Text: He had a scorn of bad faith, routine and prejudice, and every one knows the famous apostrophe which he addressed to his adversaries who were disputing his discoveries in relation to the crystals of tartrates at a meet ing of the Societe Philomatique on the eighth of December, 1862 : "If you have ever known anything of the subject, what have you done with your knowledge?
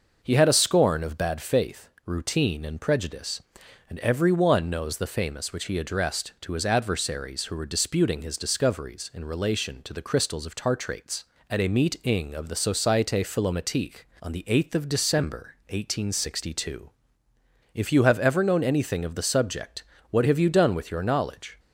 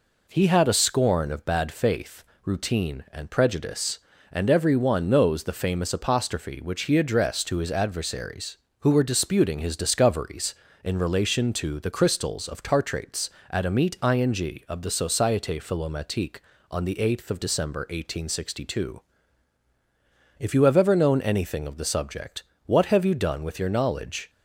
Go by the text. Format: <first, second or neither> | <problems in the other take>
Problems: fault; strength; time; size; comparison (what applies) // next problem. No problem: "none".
second | skips "apostrophe"; at 5.5 s